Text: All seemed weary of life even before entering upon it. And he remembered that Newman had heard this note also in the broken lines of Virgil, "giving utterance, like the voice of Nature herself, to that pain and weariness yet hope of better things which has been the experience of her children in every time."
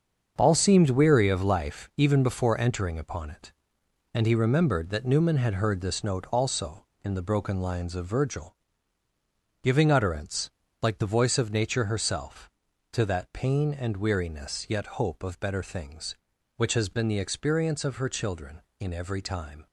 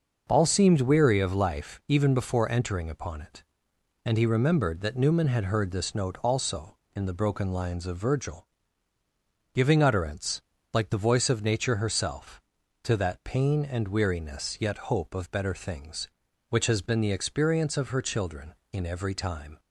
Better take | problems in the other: second | gets quieter; strong; throughout; 9 dB // starts louder than the rest; until 1.3 s; 7 dB; noticeable in the second

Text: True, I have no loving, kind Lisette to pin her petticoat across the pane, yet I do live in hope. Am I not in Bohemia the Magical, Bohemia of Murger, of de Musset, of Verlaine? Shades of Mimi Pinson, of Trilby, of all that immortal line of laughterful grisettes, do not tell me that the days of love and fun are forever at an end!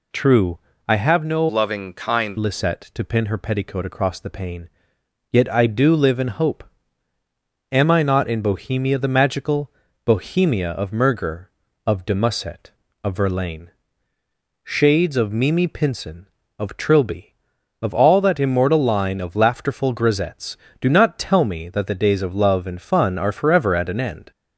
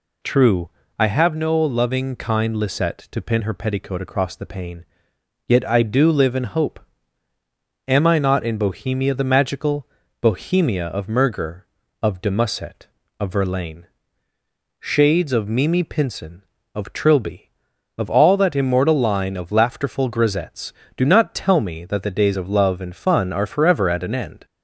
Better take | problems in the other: second | changes voice from "loving" to "kind"; from 1.4 to 2.3 s; 0.9 s long

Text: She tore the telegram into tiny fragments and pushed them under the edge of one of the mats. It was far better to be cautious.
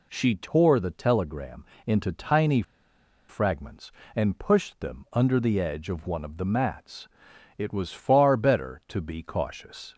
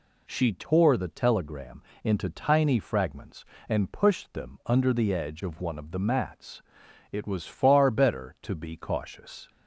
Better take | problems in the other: second | pauses between "telegram" and "into"; slight; at 1.6 s; 0.22 s long; slight in the second // pauses between "tiny" and "fragments"; noticeable; at 2.6 s; 0.66 s long

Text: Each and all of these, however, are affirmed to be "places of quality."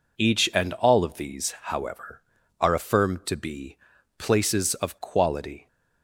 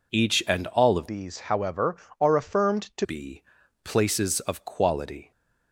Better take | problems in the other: first | changes voice from "these" to "to"; from 1.0 to 3.0 s; 2.0 s long // pauses between "be" and "places"; at 3.4 s; 0.42 s long; also in the first

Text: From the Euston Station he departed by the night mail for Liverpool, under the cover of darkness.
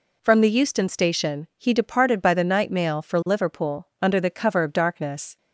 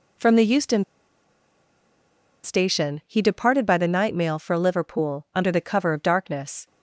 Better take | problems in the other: first | pauses between "Euston" and "Station"; strong; at 0.8 s; 1.6 s long

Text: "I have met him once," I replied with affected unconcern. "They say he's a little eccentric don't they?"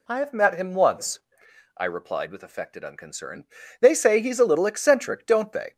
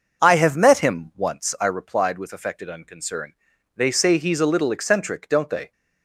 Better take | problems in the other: neither | none

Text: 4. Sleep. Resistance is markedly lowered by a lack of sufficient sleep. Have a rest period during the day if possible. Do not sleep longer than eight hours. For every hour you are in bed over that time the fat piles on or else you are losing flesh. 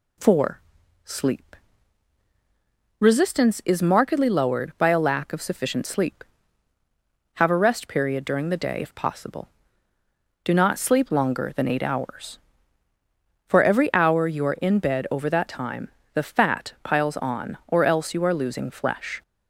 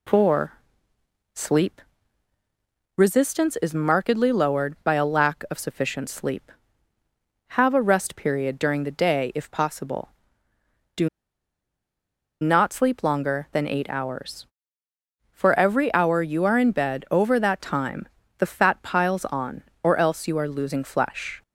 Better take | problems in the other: first | pauses between "Do" and "not"; strong; at 11.0 s; 1.3 s long // pauses between "time" and "the"; slight; at 18.0 s; 0.30 s long; slight in the first

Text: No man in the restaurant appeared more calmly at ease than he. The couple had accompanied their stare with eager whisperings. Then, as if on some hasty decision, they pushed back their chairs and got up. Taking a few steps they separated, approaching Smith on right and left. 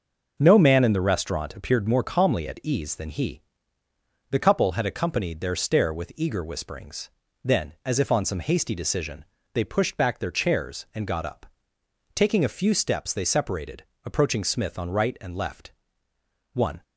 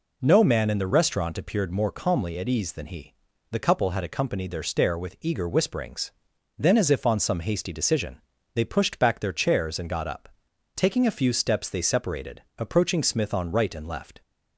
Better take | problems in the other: second | goes on to say "One"; slight; from 16.5 s on; 0.30 s long

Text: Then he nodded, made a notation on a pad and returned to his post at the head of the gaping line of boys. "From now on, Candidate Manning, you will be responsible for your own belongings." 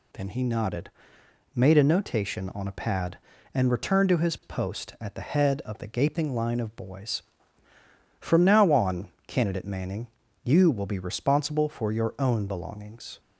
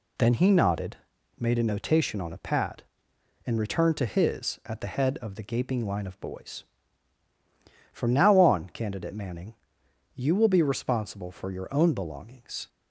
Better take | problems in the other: first | skips "post"; at 4.6 s

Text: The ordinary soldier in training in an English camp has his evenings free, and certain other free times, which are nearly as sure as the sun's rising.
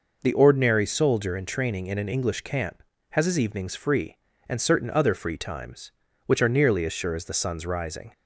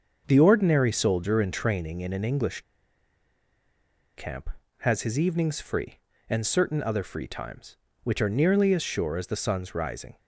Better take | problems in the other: first | starts louder than the rest; until 1.2 s; 6.5 dB // pauses between "English" and "camp"; strong; at 2.6 s; 1.5 s long

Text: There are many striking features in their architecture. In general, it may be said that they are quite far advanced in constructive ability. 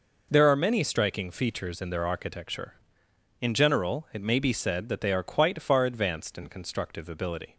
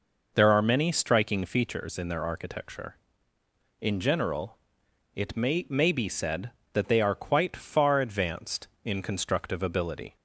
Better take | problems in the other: first | says "may" twice; at 5.6 s

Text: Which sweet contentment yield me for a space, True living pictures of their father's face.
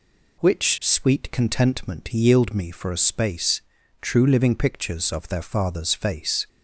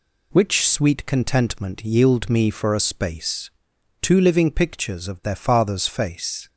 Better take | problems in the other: first | says "Two" for "True"; at 3.9 s

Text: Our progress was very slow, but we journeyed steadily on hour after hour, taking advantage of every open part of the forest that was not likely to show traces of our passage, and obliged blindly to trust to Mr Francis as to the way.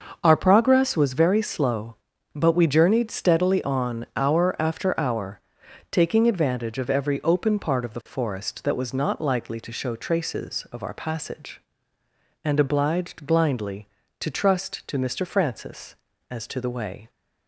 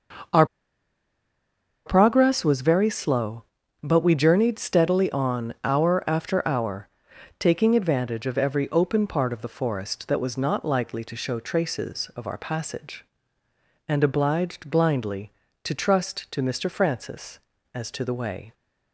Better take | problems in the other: first | starts louder than the rest; until 2.7 s; 6.5 dB; also in the first // pauses between "Our" and "progress"; strong; at 0.4 s; 1.4 s long

